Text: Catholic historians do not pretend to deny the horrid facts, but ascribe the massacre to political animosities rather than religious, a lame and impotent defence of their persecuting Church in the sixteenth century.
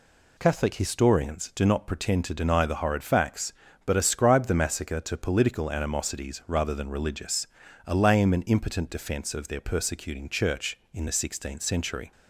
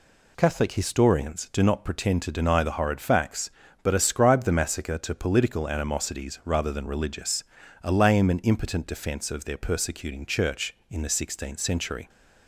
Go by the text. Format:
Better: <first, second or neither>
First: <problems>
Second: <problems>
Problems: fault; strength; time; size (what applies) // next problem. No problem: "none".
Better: neither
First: none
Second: none